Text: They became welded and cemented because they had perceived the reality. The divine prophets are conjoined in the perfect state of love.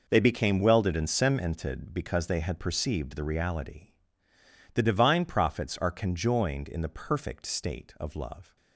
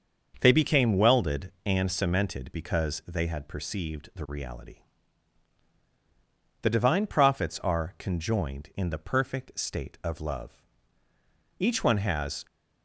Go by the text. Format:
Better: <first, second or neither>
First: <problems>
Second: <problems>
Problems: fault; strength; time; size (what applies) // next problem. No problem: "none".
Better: first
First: none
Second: starts louder than the rest; until 1.4 s; 6.5 dB // goes on to say "Each one has"; noticeable; from 11.5 s on; 0.86 s long